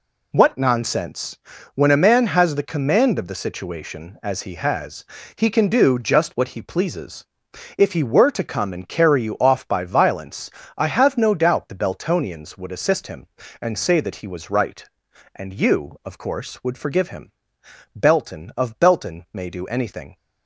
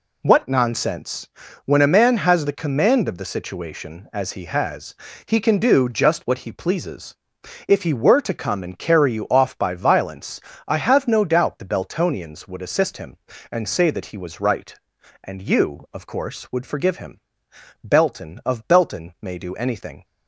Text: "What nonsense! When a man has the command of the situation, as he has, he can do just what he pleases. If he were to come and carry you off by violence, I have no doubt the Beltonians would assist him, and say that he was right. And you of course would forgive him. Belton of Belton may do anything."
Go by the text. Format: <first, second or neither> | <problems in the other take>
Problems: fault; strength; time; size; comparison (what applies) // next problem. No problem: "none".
neither | none